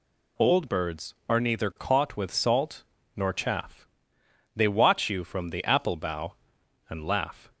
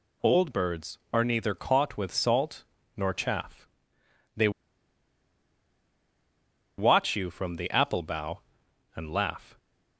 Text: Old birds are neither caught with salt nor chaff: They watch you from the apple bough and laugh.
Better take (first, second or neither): first